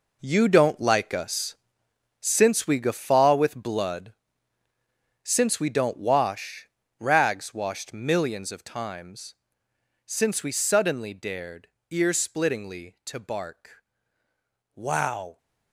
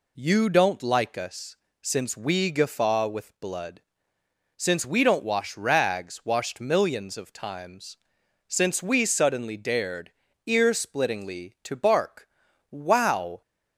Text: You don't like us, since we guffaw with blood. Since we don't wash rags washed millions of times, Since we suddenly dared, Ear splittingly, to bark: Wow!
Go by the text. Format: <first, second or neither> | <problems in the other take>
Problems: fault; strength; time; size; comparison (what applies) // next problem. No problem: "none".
second | gets quieter; strong; throughout; 11 dB // pauses between "wash" and "rags"; slight; at 6.6 s; 0.32 s long